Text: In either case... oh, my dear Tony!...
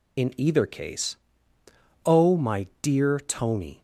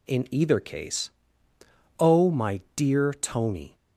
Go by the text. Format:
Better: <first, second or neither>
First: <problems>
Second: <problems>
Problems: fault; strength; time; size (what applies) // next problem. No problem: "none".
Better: second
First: loses the start of "In"; at 0.1 s; 45 ms // pauses between "my" and "dear"; slight; at 2.6 s; 0.16 s long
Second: pauses between "my" and "dear"; slight; at 2.6 s; 0.16 s long